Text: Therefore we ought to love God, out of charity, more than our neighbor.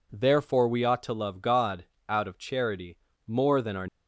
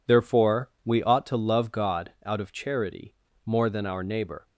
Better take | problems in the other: second | stops before "neighbor"; at 3.8 s

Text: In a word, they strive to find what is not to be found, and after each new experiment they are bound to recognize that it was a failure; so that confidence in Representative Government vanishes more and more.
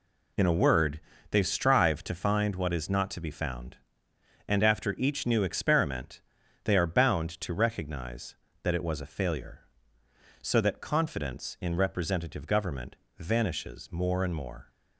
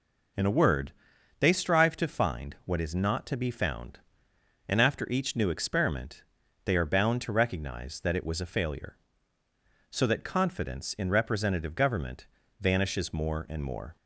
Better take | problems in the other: neither | pauses between "experiment" and "they"; the same in both // pauses between "Government" and "vanishes"; slight; the same in both

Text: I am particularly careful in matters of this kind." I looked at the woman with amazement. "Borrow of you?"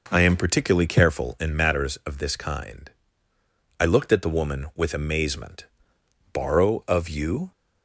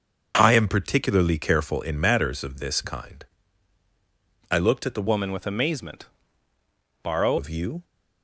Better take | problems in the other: first | starts louder than the rest; until 1.3 s; 6.5 dB // changes voice from "woman" to "Borrow"; from 5.0 to 7.3 s; 2.3 s long

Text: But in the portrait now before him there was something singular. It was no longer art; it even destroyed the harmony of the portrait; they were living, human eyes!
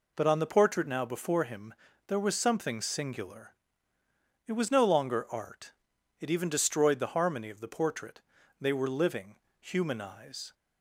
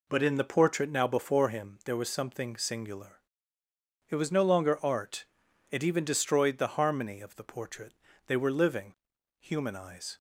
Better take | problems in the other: second | says "on" for "in"; at 0.2 s // pauses between "him" and "there"; slight; at 1.7 s; 0.34 s long

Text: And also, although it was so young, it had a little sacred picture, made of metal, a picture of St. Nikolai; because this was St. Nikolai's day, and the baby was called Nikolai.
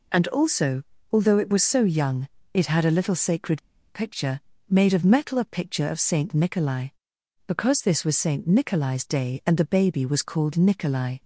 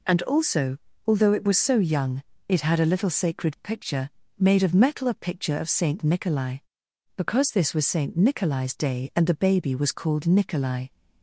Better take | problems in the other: second | pauses between "sacred" and "picture"; slight; at 3.6 s; 0.30 s long

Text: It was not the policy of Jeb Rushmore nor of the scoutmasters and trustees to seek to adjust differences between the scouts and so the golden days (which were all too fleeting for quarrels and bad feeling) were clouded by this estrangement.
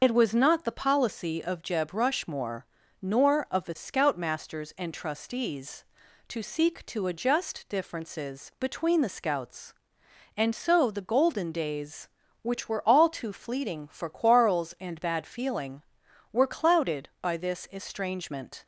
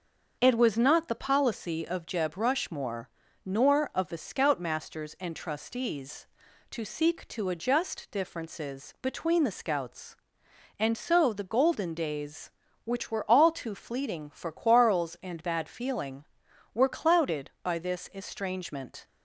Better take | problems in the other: second | loses the start of "It"; at 0.0 s; 55 ms // starts louder than the rest; until 1.0 s; 6 dB; also in the second // pauses between "Rushmore" and "nor"; at 2.6 s; 0.40 s long; also in the second

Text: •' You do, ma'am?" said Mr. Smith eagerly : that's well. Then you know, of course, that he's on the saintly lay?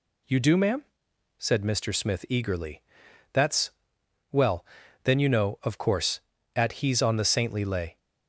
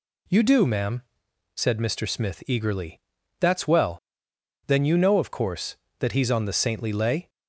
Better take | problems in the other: second | pauses between "that's" and "well"; noticeable; at 3.7 s; 0.60 s long // says "at" for "that"; at 6.5 s

